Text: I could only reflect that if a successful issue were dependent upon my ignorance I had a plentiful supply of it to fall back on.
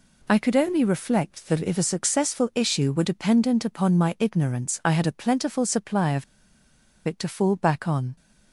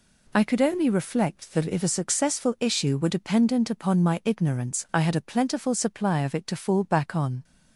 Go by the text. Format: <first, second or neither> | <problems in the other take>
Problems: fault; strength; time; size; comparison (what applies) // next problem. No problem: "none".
second | pauses between "of" and "it"; noticeable; at 6.2 s; 0.81 s long